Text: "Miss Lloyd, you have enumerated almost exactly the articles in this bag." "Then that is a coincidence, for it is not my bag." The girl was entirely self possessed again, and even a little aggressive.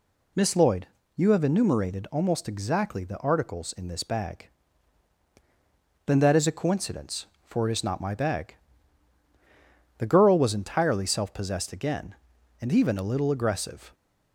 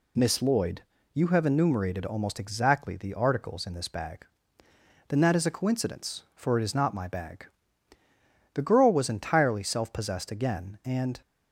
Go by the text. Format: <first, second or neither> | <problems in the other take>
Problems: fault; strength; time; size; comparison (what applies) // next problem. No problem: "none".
first | stops before "even a little aggressive"; at 11.2 s